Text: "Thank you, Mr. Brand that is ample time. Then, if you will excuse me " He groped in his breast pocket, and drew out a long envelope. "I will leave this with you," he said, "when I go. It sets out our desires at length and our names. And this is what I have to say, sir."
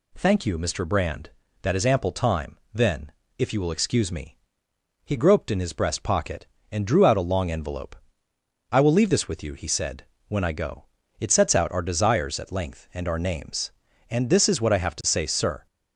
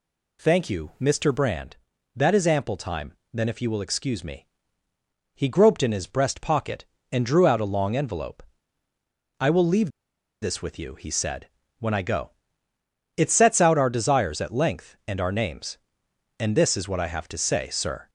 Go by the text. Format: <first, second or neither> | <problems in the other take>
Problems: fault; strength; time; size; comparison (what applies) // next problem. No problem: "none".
first | pauses between "leave" and "this"; noticeable; at 9.8 s; 0.51 s long